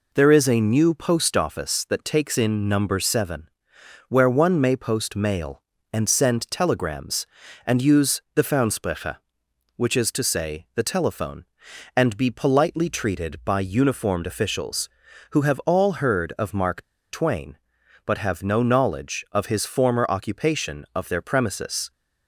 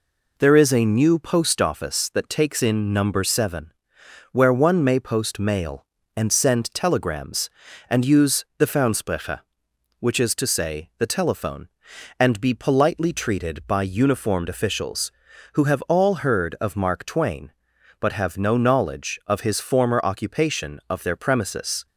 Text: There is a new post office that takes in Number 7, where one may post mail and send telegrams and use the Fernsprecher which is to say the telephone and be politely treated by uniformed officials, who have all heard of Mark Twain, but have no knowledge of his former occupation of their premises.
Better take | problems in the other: second | pauses between "Mark" and "Twain"; slight; at 16.8 s; 0.28 s long

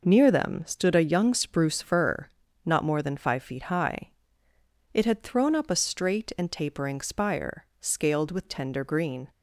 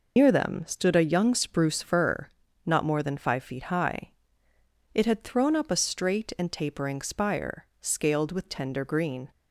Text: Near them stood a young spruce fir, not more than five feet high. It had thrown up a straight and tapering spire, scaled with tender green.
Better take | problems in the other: first | loses the start of "Near"; at 0.1 s; 130 ms

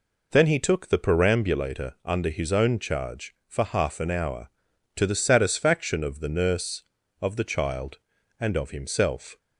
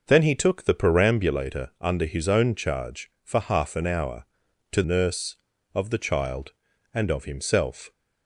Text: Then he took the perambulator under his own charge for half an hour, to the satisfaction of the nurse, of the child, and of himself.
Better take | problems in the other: first | skips "the satisfaction of the"; at 4.8 s

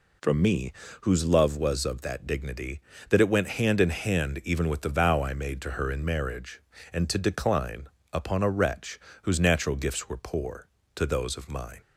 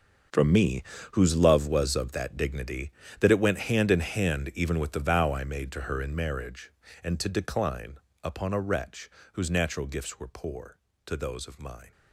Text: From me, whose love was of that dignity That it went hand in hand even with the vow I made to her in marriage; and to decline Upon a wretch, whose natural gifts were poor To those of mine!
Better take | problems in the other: first | gets quieter; strong; throughout; 14 dB // pauses between "decline" and "Upon"; slight; at 7.9 s; 0.24 s long; slight in the first

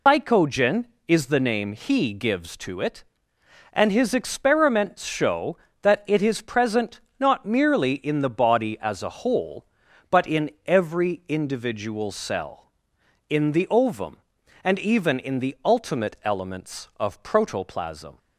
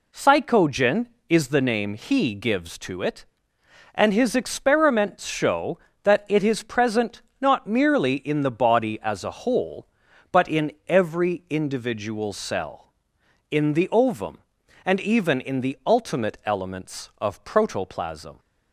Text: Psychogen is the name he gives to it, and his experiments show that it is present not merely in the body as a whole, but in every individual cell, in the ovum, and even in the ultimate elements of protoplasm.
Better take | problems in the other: second | loses the start of "Psychogen"; at 0.0 s; 140 ms // pauses between "present" and "not"; slight; at 6.9 s; 0.18 s long; slight in the second // pauses between "in" and "every"; slight; at 10.4 s; 0.16 s long; slight in the second

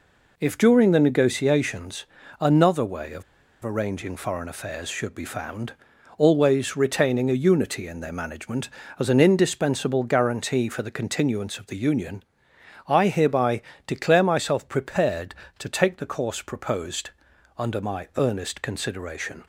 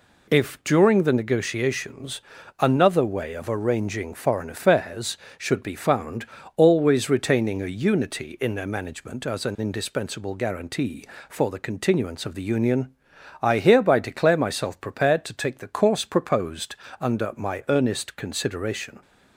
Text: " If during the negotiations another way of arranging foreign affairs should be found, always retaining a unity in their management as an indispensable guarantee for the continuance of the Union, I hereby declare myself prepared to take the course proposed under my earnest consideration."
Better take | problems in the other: second | pauses between "negotiations" and "another"; slight; at 2.0 s; 0.36 s long; also in the second // pauses between "of" and "arranging"; at 3.2 s; 0.40 s long // pauses between "hereby" and "declare"; slight; at 13.6 s; 0.24 s long // pauses between "proposed" and "under"; noticeable; at 17.1 s; 0.46 s long; slight in the second

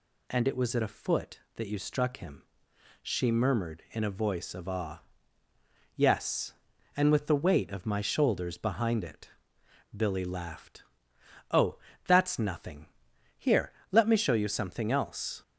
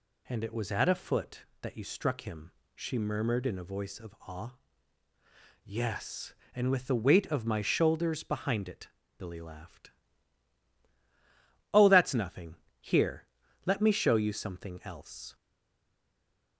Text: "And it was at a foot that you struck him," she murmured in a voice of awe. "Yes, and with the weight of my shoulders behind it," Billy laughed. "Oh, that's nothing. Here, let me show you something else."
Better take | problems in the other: first | stays silent after the last word; noticeable; from 15.3 s on; 1.2 s long

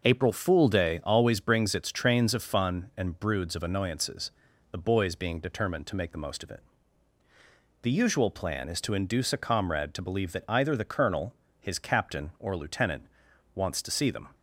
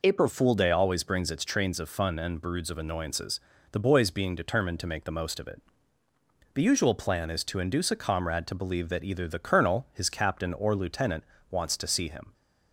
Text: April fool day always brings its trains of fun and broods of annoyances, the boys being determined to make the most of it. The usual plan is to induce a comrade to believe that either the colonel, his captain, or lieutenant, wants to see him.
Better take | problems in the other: second | says "them" for "him"; at 14.1 s

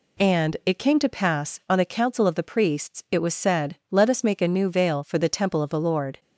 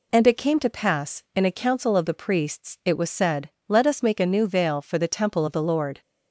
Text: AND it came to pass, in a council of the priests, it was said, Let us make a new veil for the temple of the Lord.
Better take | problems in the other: second | says "on" for "in"; at 1.6 s

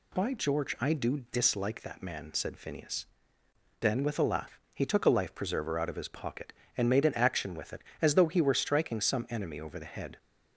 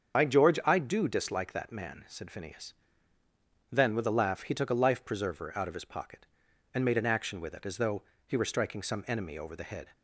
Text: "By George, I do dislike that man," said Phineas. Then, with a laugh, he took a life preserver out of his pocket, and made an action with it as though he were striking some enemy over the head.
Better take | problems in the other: first | loses the start of "By"; at 0.1 s; 60 ms // starts louder than the rest; strong; until 1.2 s; 7 dB // pauses between "though" and "he"; slight; at 8.0 s; 0.22 s long

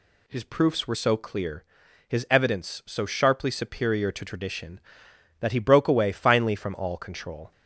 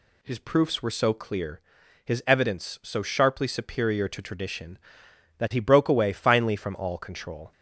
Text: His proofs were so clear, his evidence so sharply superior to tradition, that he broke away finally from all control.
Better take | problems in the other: neither | none

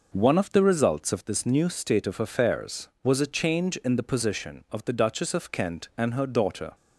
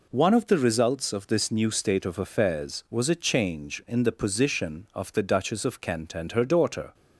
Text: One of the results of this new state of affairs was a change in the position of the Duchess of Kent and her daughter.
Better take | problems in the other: neither | none

